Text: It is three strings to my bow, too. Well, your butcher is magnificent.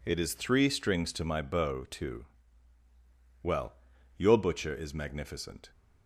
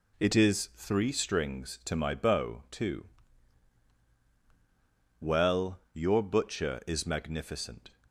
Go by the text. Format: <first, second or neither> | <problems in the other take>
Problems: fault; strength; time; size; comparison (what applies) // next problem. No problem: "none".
neither | none